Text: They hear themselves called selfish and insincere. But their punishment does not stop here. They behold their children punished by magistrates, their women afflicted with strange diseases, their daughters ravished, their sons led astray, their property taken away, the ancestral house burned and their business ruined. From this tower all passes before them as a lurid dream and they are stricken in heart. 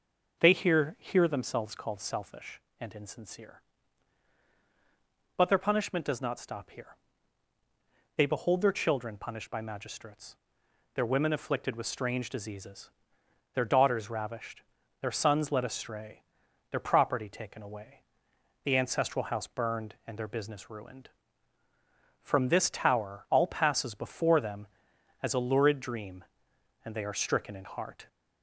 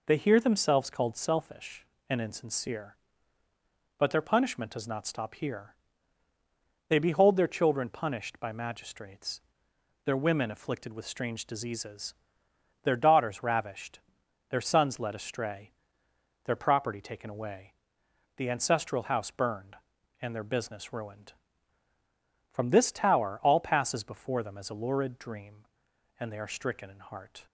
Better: second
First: says "hear" twice; at 0.9 s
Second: none

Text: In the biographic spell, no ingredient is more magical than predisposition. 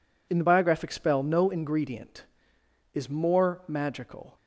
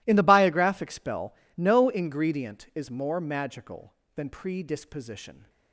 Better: second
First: stops before "than predisposition"; at 4.3 s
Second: none

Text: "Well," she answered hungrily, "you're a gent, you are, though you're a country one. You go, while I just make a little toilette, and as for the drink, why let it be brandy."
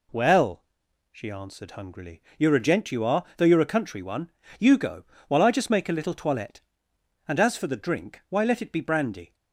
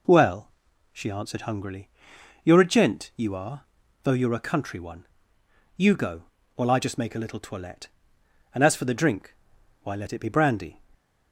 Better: neither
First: none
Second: none

